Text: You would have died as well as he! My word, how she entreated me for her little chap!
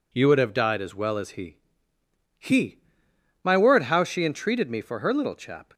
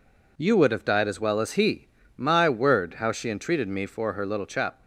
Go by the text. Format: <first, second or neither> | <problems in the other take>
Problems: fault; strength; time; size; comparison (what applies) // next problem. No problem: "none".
second | says "he" twice; at 2.3 s